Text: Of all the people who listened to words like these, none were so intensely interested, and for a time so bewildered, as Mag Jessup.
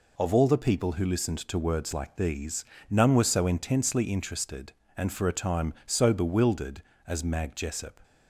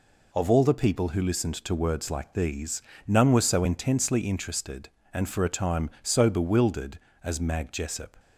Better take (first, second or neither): neither